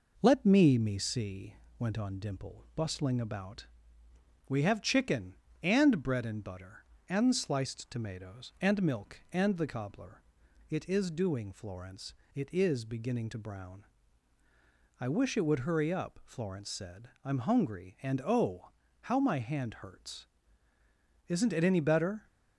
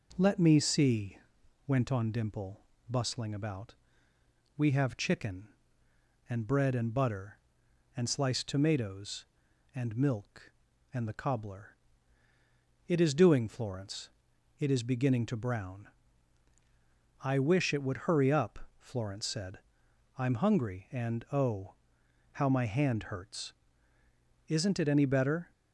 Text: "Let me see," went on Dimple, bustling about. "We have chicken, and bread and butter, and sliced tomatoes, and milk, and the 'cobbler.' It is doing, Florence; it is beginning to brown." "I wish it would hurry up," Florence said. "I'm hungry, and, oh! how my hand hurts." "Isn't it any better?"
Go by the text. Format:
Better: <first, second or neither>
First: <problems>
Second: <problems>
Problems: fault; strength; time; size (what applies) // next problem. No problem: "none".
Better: second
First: says "me" twice; at 0.7 s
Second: none